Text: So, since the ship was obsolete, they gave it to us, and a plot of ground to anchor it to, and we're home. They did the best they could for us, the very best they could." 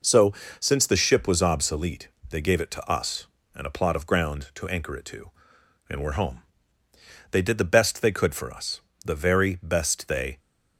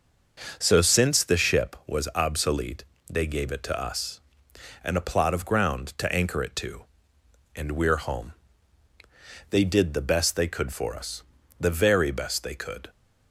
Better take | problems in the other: second | stops before "could"; at 10.3 s

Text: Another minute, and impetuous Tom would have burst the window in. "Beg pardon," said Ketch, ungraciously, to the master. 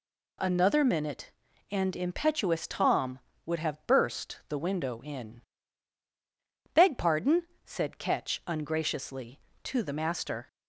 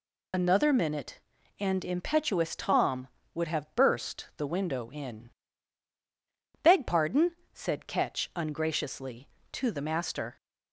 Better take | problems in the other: first | loses the start of "Another"; at 0.3 s; 70 ms

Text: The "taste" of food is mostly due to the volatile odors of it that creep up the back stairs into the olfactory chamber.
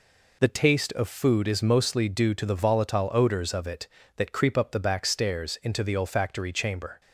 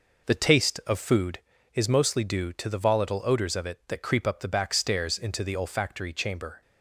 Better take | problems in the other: first | starts louder than the rest; noticeable; until 1.3 s; 5 dB

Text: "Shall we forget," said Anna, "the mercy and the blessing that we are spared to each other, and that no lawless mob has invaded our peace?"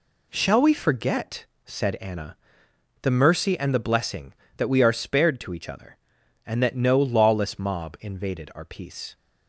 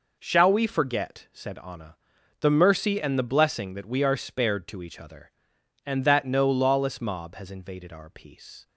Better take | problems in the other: second | skips "has"; at 7.9 s

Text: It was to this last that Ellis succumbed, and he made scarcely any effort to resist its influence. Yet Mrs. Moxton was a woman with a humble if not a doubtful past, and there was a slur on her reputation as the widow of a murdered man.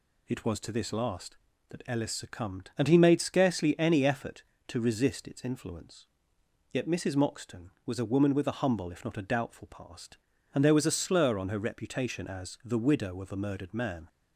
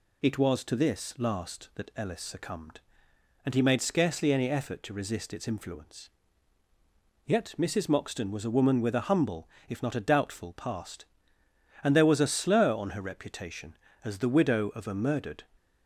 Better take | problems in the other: first | pauses between "humble" and "if"; slight; at 9.4 s; 0.22 s long // stops before "man"; at 15.5 s

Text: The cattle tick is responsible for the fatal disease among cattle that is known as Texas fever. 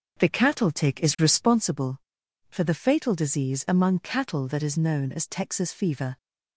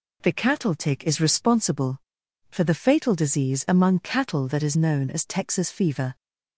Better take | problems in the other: second | starts louder than the rest; noticeable; until 1.7 s; 6 dB

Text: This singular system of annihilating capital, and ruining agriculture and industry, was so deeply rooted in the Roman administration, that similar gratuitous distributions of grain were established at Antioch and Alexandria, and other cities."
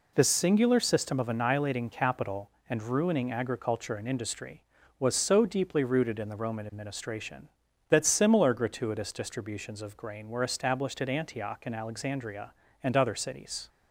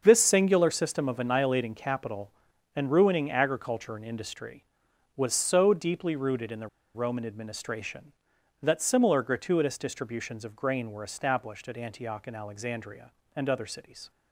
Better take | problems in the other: first | starts louder than the rest; until 1.0 s; 6.5 dB // pauses between "the" and "Roman"; slight; at 6.6 s; 0.28 s long

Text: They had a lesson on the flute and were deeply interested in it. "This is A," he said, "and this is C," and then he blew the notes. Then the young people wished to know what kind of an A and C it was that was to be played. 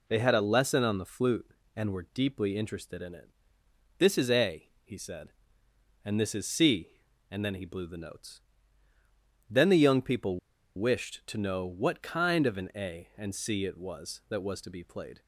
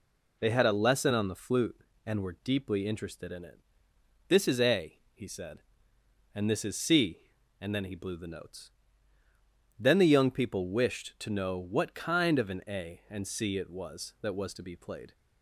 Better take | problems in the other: second | pauses between "people" and "wished"; at 10.3 s; 0.38 s long

